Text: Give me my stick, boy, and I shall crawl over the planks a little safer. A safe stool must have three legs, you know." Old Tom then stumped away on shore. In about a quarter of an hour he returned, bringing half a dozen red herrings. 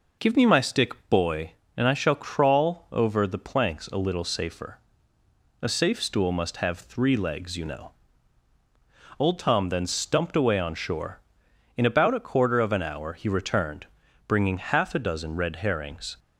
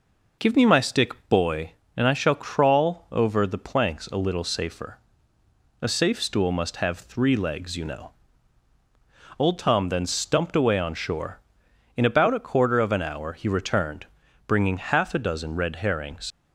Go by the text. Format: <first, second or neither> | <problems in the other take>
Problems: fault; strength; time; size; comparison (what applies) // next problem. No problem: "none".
first | leaves "herrings" unfinished; at 16.3 s; 80 ms